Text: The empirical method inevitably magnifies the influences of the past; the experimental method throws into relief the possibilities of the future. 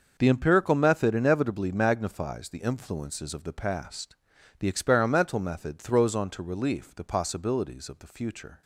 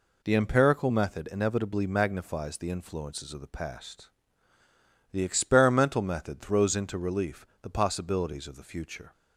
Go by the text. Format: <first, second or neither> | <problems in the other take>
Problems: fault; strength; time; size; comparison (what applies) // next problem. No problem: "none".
second | starts louder than the rest; until 1.1 s; 6.5 dB // says "onto" for "into"; at 6.1 s